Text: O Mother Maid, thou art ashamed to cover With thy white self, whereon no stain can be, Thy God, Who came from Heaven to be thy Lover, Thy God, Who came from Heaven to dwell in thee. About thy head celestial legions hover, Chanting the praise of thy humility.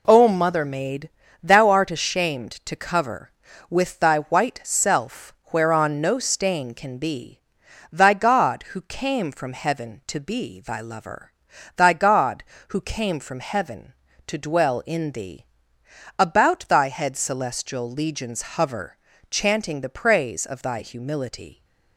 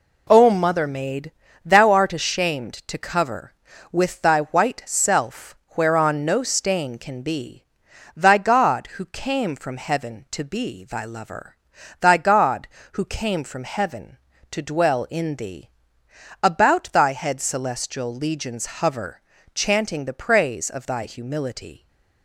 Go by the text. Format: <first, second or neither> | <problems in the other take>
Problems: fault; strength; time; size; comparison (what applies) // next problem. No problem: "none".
neither | pauses between "legions" and "hover"; slight; the same in both